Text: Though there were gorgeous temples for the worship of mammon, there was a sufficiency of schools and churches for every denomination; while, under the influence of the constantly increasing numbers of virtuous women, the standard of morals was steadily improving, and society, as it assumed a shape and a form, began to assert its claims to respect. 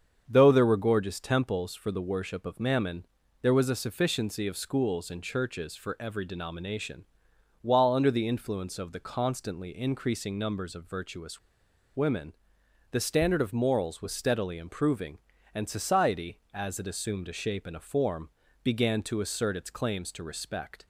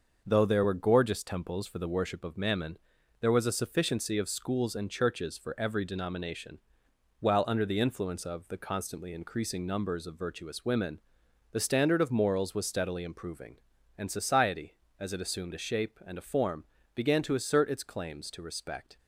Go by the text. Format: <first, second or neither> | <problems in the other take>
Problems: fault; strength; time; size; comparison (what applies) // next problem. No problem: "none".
second | starts louder than the rest; strong; until 1.2 s; 7 dB; also in the second // pauses between "virtuous" and "women"; noticeable; at 11.3 s; 0.56 s long